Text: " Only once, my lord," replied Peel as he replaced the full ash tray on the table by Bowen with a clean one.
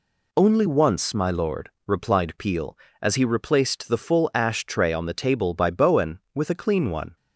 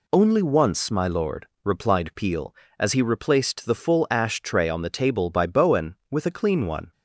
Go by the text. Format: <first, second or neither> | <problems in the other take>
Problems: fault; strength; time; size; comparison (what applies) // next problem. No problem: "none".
neither | none